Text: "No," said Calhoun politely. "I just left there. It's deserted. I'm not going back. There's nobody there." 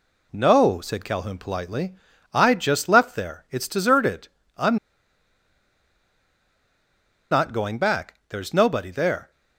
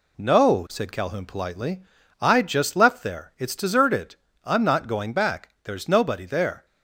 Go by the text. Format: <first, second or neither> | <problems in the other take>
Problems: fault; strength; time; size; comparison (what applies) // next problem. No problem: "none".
second | pauses between "I'm" and "not"; strong; at 4.7 s; 2.5 s long